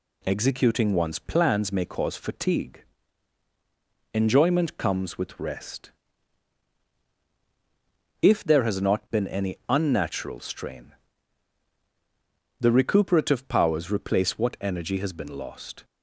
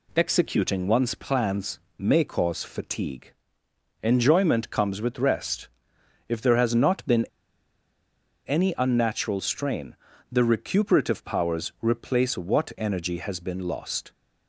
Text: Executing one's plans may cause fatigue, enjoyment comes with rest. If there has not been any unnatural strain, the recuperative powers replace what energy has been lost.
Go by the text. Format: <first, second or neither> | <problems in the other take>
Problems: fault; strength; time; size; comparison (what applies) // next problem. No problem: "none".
first | pauses between "plans" and "may"; slight; at 1.7 s; 0.18 s long // pauses between "been" and "any"; at 7.2 s; 1.1 s long